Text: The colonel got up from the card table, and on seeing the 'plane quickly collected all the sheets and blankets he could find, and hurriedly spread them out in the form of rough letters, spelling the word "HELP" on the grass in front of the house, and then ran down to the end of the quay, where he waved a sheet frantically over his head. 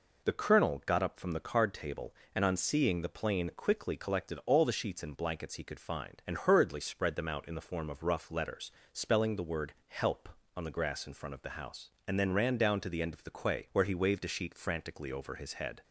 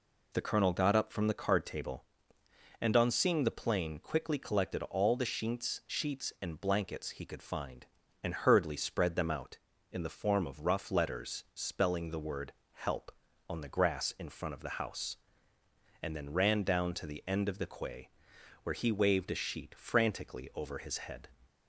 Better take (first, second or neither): first